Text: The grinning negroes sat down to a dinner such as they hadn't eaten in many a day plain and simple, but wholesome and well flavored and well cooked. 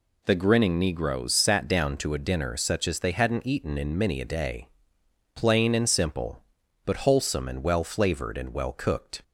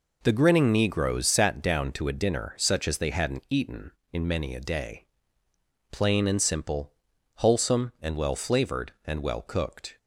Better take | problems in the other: first | pauses between "day" and "plain"; noticeable; at 5.0 s; 0.86 s long; noticeable in the first // skips "but"; at 7.1 s

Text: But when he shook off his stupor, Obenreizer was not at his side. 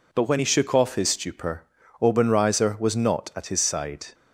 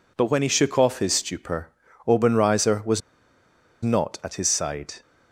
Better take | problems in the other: first | pauses between "was" and "not"; noticeable; at 3.0 s; 0.82 s long

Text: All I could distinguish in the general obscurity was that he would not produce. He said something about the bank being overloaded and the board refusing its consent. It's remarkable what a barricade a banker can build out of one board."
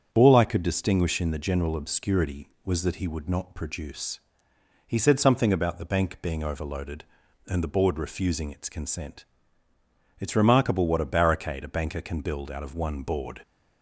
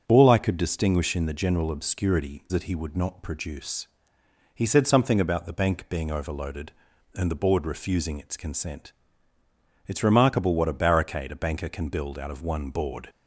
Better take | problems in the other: first | starts louder than the rest; until 1.0 s; 7 dB; strong in the first // skips "was"; at 2.4 s

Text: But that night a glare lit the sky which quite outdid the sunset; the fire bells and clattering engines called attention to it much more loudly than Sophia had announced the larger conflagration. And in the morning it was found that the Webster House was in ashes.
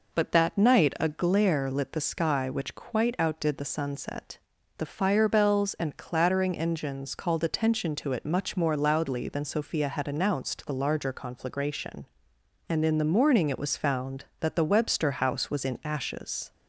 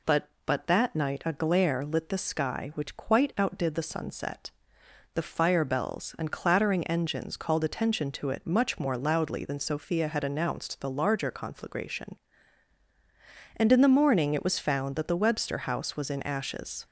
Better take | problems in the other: first | says "But" twice; at 0.4 s

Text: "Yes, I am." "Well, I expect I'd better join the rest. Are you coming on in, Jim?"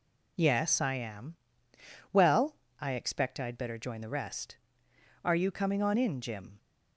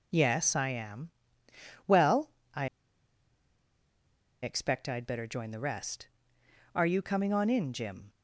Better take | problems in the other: first | pauses between "I" and "expect"; strong; at 2.6 s; 1.7 s long

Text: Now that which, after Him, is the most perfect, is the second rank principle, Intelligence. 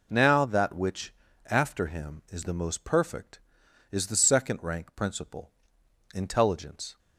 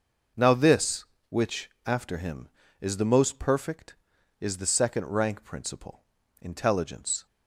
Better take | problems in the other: first | says "this" for "that"; at 0.5 s

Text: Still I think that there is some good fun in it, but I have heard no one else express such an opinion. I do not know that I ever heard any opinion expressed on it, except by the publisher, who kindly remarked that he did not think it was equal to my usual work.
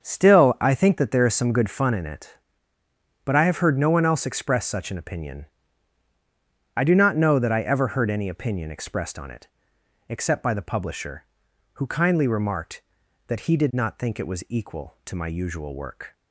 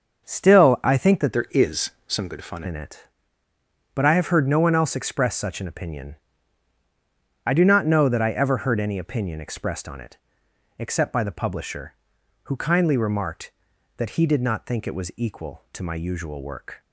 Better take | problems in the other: first | starts louder than the rest; until 1.2 s; 6.5 dB; also in the first // changes voice from "there" to "fun"; from 1.3 to 2.6 s; 1.3 s long // pauses between "is" and "some"; slight; at 1.8 s; 0.16 s long

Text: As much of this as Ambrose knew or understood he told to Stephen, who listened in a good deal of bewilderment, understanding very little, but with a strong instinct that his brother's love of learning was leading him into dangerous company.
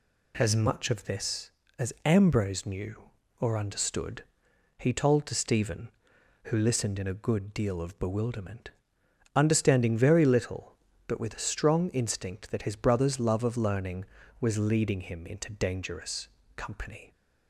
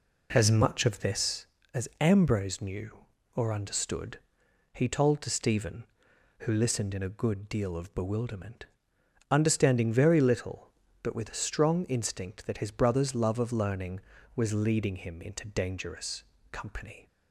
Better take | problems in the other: first | starts louder than the rest; slight; until 1.7 s; 3.5 dB // pauses between "understood" and "he"; noticeable; at 4.1 s; 0.54 s long; noticeable in the first // pauses between "dangerous" and "company"; slight; at 16.2 s; 0.30 s long; slight in the first

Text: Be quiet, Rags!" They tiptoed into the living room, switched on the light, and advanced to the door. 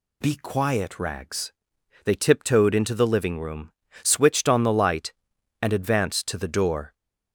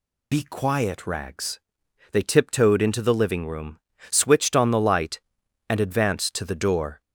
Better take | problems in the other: first | loses the start of "Be"; at 0.3 s; 25 ms

